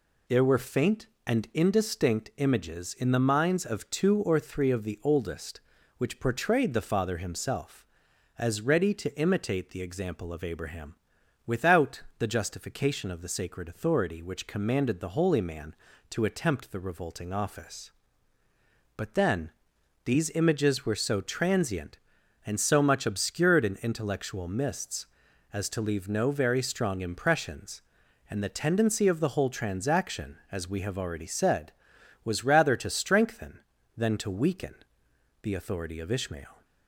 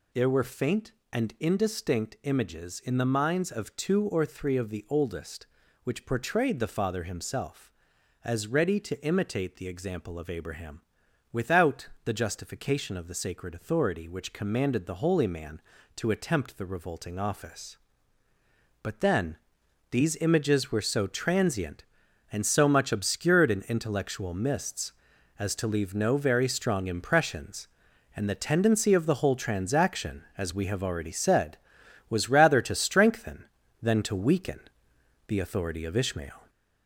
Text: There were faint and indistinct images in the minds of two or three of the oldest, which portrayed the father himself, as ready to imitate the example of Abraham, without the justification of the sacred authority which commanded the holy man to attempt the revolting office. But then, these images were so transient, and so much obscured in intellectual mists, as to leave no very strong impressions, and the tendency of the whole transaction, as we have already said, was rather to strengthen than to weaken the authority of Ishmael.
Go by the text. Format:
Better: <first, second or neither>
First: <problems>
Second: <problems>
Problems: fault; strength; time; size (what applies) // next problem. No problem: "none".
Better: first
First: pauses between "without" and "the"; slight; at 12.0 s; 0.16 s long // pauses between "weaken" and "the"; noticeable; at 34.7 s; 0.68 s long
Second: gets louder; noticeable; throughout; 4.5 dB // pauses between "without" and "the"; slight; at 11.8 s; 0.16 s long // pauses between "weaken" and "the"; noticeable; at 34.5 s; 0.68 s long